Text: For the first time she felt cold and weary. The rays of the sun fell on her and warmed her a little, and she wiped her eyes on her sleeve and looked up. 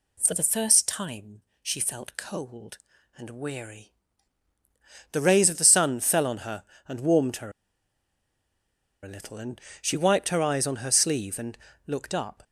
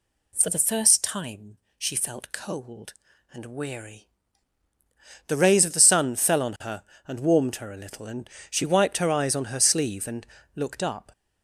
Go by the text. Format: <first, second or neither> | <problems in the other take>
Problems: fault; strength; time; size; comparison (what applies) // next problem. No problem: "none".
second | pauses between "time" and "she"; slight; at 1.4 s; 0.20 s long; slight in the second // pauses between "her" and "a"; strong; at 7.5 s; 1.5 s long // pauses between "and" and "she"; slight; at 9.5 s; 0.22 s long; slight in the second // pauses between "and" and "looked"; slight; at 11.5 s; 0.30 s long; slight in the second